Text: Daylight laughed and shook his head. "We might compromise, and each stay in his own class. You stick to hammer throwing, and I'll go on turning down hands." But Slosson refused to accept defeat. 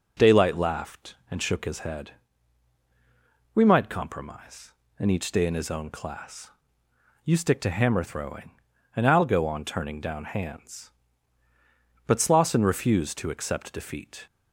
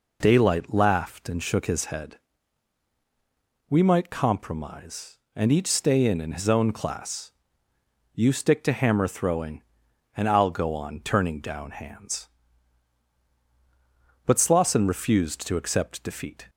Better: first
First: none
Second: says "in" twice; at 6.2 s

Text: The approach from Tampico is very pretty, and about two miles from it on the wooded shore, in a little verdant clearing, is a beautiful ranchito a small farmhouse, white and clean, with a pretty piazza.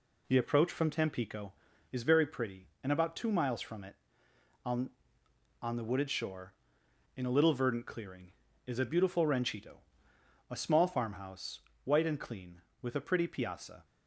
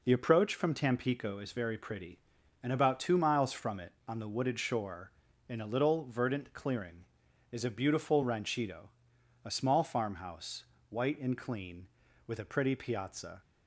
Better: second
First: says "on" twice; at 5.6 s // pauses between "ranchito" and "a"; noticeable; at 9.7 s; 0.74 s long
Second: pauses between "ranchito" and "a"; noticeable; at 8.8 s; 0.56 s long

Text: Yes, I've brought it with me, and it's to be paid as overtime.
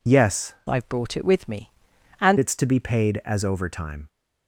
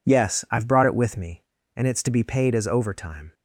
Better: second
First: changes voice from "I've" to "and"; from 0.6 to 2.3 s; 1.7 s long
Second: none

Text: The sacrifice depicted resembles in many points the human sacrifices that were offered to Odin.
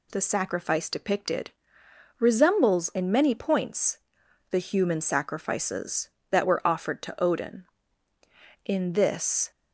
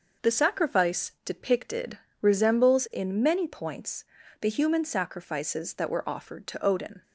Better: second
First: pauses between "depicted" and "resembles"; noticeable; at 1.5 s; 0.68 s long // pauses between "points" and "the"; noticeable; at 3.9 s; 0.52 s long // goes on to say "In this"; noticeable; from 8.6 s on; 0.86 s long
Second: pauses between "depicted" and "resembles"; slight; at 1.9 s; 0.24 s long // pauses between "points" and "the"; slight; at 4.0 s; 0.36 s long

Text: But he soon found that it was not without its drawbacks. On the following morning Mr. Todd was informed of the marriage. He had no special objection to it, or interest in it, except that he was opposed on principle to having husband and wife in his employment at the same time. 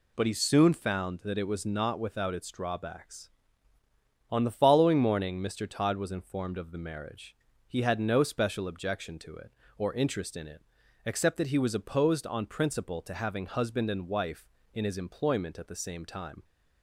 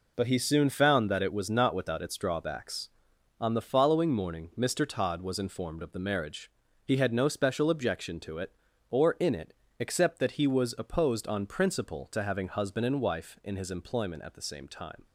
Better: first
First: none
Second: skips "interest"; at 9.1 s

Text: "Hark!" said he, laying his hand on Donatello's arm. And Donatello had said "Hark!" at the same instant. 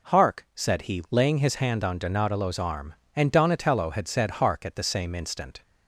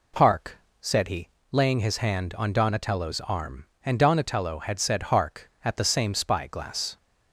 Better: first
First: none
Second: says "spyglass" for "instant"; at 6.1 s

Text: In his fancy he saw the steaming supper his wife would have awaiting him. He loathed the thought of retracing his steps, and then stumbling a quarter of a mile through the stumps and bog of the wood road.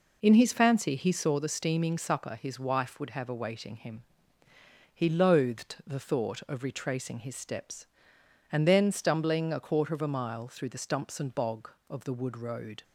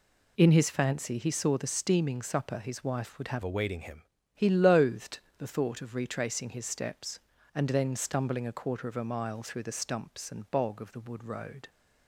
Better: first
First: none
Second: changes voice from "awaiting" to "him"; from 3.4 to 4.0 s; 0.6 s long // pauses between "loathed" and "the"; slight; at 5.1 s; 0.22 s long

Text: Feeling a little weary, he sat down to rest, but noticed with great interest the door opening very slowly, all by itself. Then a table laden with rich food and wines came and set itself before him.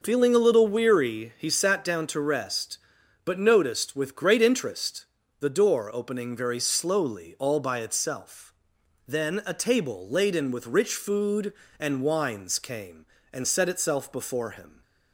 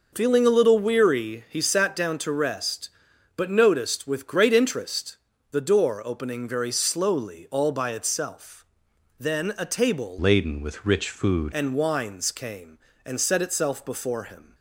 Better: first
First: pauses between "interest" and "the"; slight; at 5.0 s; 0.34 s long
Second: pauses between "interest" and "the"; slight; at 5.1 s; 0.34 s long // changes voice from "laden" to "food"; from 10.1 to 11.5 s; 1.4 s long

